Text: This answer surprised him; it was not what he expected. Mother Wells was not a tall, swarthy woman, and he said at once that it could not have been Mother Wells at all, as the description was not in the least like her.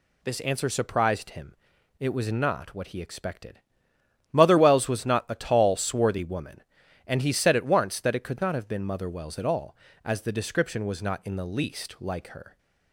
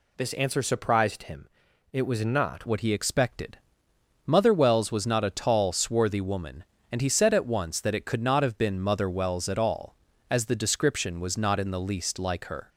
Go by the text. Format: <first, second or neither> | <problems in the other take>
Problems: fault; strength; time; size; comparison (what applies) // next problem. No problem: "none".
first | changes voice at "what"; from 2.6 s on; 10.0 s long